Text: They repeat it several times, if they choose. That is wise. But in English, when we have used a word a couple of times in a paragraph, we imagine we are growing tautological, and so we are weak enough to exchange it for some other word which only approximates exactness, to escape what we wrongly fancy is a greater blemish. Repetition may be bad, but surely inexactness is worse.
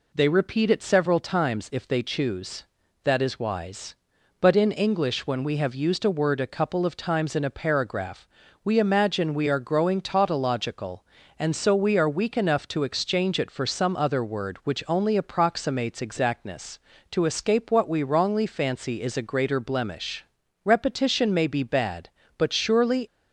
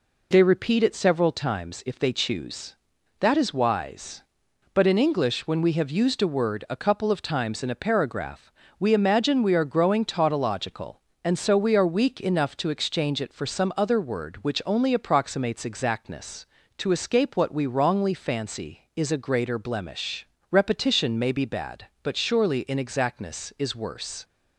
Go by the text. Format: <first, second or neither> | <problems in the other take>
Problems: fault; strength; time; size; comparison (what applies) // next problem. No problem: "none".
second | stops before "inexactness is worse"; at 23.0 s